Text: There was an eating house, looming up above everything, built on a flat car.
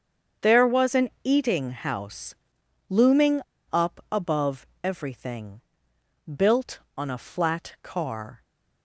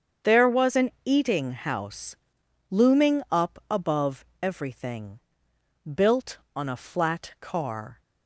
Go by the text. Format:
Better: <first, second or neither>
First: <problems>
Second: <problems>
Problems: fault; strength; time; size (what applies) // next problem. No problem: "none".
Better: second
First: starts louder than the rest; strong; until 1.5 s; 7.5 dB // pauses between "looming" and "up"; slight; at 3.4 s; 0.30 s long // pauses between "above" and "everything"; slight; at 4.6 s; 0.18 s long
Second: starts louder than the rest; strong; until 1.3 s; 7.5 dB // pauses between "above" and "everything"; slight; at 4.2 s; 0.18 s long